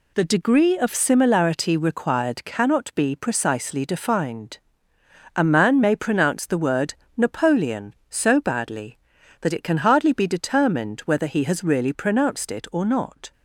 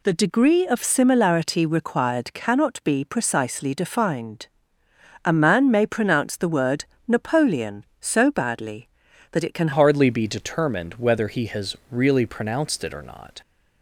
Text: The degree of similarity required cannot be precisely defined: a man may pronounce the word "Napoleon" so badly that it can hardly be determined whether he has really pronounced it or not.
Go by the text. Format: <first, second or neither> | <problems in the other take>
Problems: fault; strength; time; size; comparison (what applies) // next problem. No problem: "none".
first | pauses between "word" and "Napoleon"; slight; at 6.8 s; 0.24 s long; slight in the first // changes voice at "hardly"; from 9.7 s on; 3.7 s long // pauses between "has" and "really"; slight; at 11.7 s; 0.16 s long